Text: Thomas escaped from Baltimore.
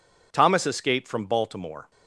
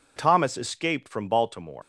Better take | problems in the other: first | leaves "Baltimore" unfinished; at 1.8 s; 155 ms

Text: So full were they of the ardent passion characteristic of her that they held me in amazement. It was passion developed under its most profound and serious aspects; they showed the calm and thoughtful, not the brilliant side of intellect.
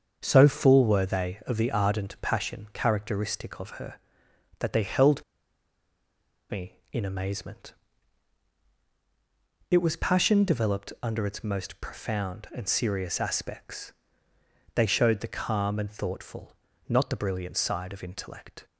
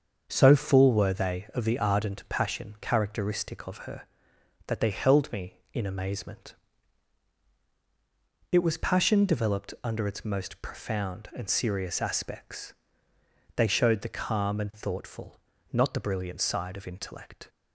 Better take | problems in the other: second | starts louder than the rest; until 1.2 s; 7 dB; also in the second // pauses between "held" and "me"; strong; at 5.2 s; 1.2 s long

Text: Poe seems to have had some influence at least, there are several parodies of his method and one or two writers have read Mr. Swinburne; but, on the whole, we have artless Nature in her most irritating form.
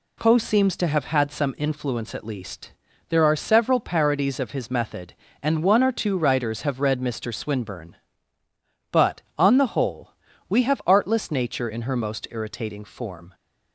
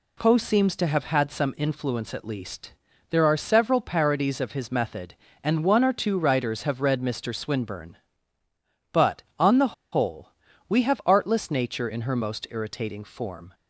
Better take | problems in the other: first | pauses between "the" and "whole"; slight; at 9.7 s; 0.17 s long

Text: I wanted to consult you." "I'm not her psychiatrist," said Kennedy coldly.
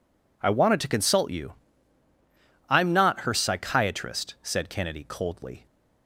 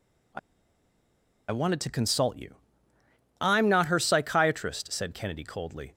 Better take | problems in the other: first | pauses between "I" and "wanted"; at 0.3 s; 1.1 s long

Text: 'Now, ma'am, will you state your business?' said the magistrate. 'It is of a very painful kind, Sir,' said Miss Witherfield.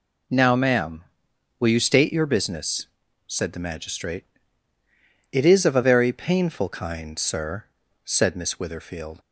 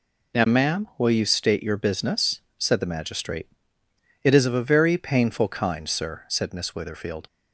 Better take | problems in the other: neither | none

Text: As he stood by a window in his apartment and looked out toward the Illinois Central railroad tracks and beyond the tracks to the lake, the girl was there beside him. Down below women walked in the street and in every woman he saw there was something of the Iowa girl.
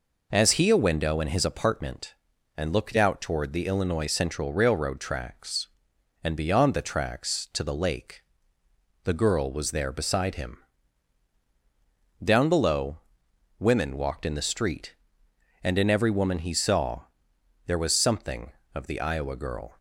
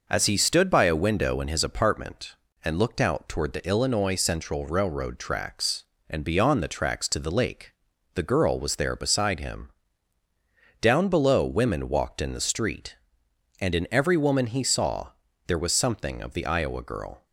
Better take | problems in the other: second | skips "stood by"; at 0.6 s // pauses between "below" and "women"; noticeable; at 12.9 s; 0.62 s long // pauses between "saw" and "there"; noticeable; at 17.0 s; 0.62 s long; also in the second

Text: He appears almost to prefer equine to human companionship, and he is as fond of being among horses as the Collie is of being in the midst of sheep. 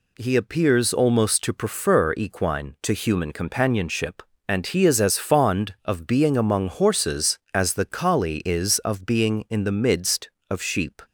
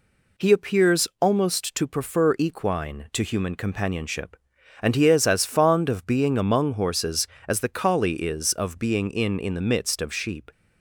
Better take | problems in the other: first | says "in" twice; at 9.3 s

